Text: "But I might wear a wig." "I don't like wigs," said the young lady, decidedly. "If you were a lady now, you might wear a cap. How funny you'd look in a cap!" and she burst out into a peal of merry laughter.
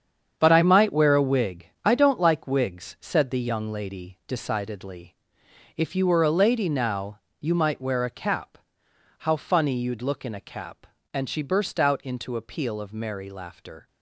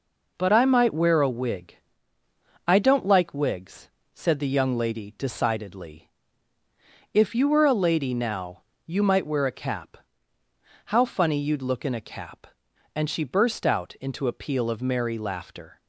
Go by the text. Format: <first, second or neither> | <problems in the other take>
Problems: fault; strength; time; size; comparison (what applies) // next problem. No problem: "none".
second | gets quieter; strong; throughout; 10.5 dB